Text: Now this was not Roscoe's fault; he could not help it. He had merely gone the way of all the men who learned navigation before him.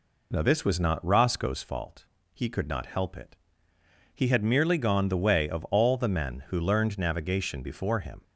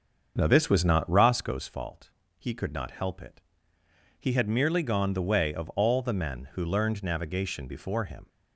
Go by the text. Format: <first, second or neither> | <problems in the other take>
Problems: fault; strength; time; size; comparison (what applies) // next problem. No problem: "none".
first | starts louder than the rest; until 1.3 s; 6.5 dB